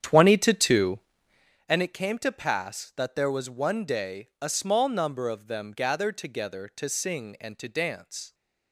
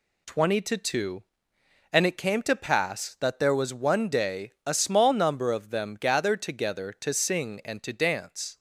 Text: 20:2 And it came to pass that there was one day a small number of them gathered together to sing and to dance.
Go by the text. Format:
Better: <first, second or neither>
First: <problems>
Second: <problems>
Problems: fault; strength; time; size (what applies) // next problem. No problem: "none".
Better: second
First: starts louder than the rest; strong; until 1.5 s; 9 dB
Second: none